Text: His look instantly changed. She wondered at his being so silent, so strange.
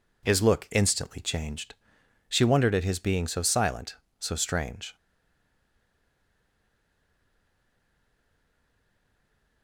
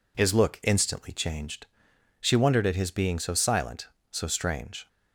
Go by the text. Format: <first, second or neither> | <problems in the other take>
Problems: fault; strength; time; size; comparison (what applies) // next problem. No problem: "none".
second | stays silent after the last word; strong; from 4.9 s on; 4.7 s long